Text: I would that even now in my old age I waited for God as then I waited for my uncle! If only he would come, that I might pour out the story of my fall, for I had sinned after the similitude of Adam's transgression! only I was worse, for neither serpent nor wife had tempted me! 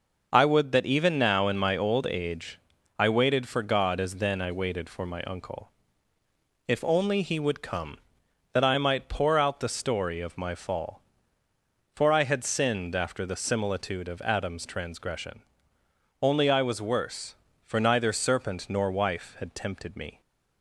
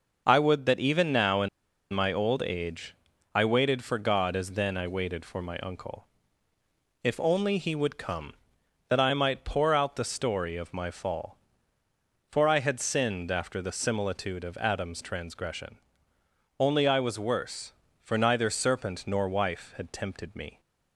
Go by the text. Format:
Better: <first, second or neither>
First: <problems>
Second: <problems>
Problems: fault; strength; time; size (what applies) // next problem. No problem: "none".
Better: first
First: pauses between "age" and "I"; at 2.5 s; 0.40 s long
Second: pauses between "in" and "my"; at 1.4 s; 0.45 s long // pauses between "age" and "I"; at 2.9 s; 0.40 s long